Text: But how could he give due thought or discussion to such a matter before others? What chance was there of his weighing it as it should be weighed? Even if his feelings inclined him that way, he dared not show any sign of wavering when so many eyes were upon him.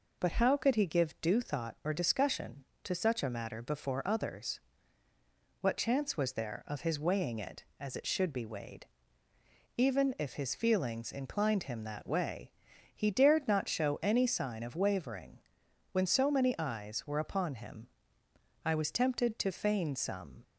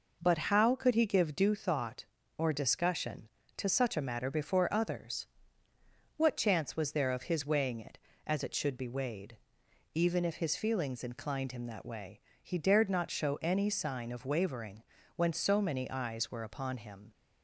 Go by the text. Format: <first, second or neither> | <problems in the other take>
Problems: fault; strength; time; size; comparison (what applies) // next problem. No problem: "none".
second | pauses between "wavering" and "when"; noticeable; at 15.3 s; 0.54 s long; slight in the second // goes on to say "I was tempted to feign some"; strong; from 18.6 s on; 1.7 s long